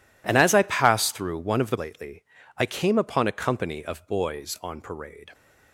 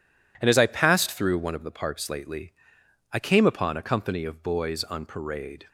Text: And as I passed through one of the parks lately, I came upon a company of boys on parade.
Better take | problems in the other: second | skips "parks"; at 1.7 s

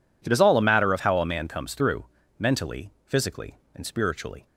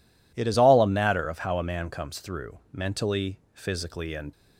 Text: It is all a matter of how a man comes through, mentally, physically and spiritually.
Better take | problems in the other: first | stops before "spiritually"; at 4.3 s

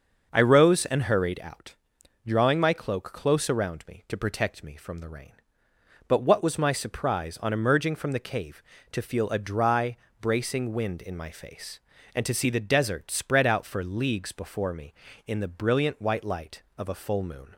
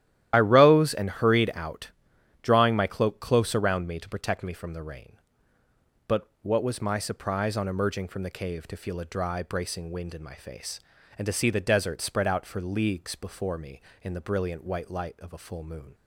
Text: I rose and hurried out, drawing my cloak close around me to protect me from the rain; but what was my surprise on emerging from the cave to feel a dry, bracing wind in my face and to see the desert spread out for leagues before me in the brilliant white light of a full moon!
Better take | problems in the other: first | loses the start of "I"; at 0.3 s; 40 ms // starts louder than the rest; strong; until 1.3 s; 12.5 dB; also in the first

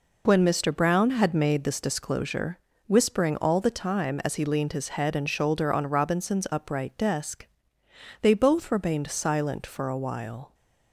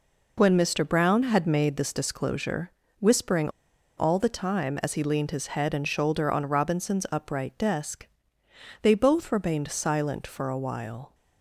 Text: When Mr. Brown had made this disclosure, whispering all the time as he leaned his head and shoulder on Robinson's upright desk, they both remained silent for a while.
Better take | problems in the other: first | pauses between "whispering" and "all"; noticeable; at 3.4 s; 0.48 s long

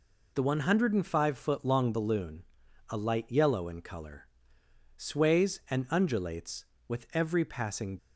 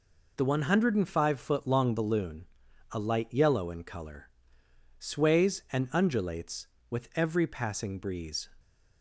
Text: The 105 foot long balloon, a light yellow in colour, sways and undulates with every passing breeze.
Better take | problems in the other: second | stops before "breeze"; at 7.9 s

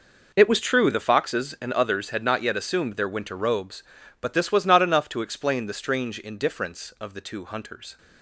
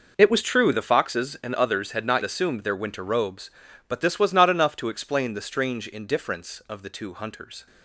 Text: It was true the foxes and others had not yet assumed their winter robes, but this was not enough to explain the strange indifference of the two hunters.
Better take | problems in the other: first | skips "yet"; at 2.2 s

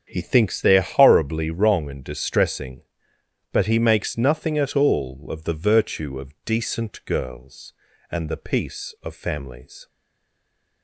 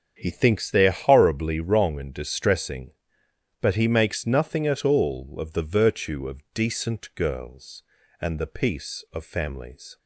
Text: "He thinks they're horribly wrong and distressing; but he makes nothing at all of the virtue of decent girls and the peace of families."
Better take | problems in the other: second | starts louder than the rest; strong; until 1.0 s; 7 dB; strong in the second // stays silent after the last word; from 9.8 s on; 1.0 s long

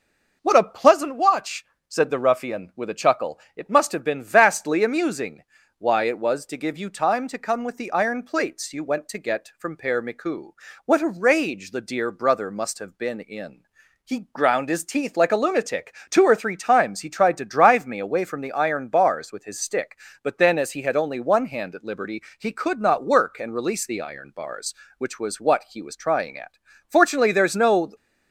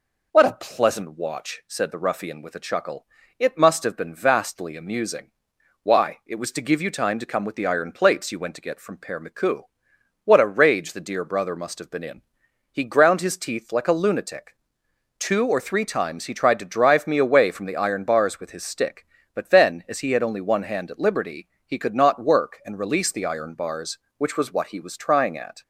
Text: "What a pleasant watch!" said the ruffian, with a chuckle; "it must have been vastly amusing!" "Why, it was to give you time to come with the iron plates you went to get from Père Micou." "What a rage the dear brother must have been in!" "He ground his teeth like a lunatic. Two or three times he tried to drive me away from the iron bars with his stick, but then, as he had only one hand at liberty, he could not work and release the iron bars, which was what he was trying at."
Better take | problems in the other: second | goes on to say "Fortunately there's no"; noticeable; from 26.8 s on; 1.0 s long

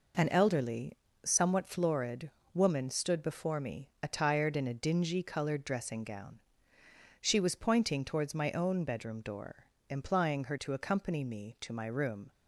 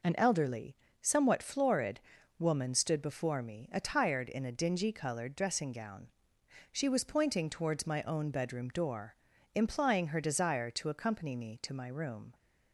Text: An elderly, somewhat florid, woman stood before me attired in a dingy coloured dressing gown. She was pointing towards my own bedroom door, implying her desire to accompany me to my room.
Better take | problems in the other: second | skips "desire"; at 10.5 s

